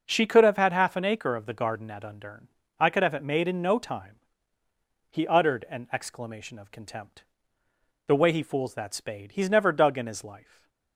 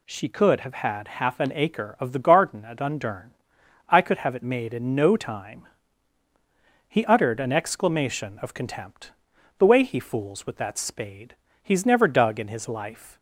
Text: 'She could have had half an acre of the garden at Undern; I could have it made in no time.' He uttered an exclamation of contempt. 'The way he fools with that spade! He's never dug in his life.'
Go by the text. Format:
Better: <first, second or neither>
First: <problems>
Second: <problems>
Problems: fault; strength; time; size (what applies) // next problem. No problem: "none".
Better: second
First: skips "with"; at 8.7 s // stays silent after the last word; slight; from 10.3 s on; 0.6 s long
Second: none